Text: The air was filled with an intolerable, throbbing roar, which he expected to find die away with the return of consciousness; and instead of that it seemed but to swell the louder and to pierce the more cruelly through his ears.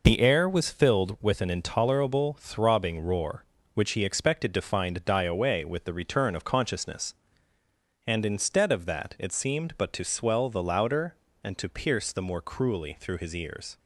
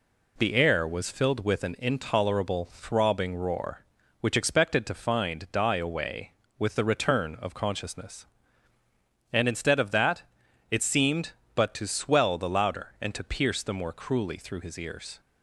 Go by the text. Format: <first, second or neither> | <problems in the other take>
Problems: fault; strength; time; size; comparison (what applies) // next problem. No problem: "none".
first | skips "he"; at 4.3 s // pauses between "that" and "it"; noticeable; at 10.2 s; 0.48 s long